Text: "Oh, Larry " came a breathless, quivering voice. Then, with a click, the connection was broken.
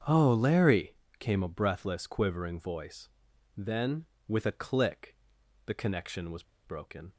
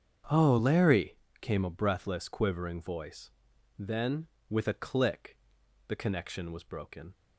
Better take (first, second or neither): second